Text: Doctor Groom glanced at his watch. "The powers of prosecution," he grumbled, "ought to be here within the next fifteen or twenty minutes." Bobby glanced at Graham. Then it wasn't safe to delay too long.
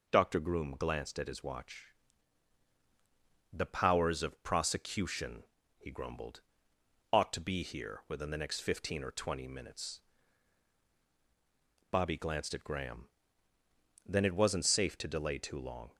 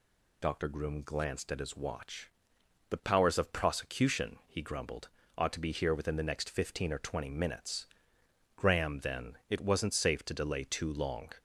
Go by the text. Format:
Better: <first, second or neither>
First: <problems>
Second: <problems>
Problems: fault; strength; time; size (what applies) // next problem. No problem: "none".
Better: first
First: none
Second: skips "Bobby glanced at"; at 8.2 s